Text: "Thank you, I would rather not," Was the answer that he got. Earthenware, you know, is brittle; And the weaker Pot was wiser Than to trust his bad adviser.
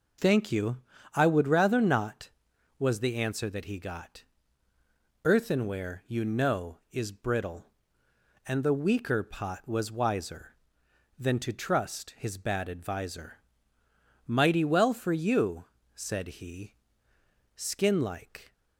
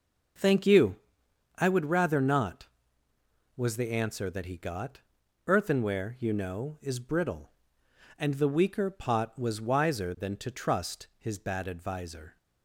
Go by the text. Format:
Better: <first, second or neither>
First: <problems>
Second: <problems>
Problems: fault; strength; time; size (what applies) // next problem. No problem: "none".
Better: second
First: goes on to say "Mighty well for you said he Skin like"; strong; from 14.2 s on; 4.2 s long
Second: none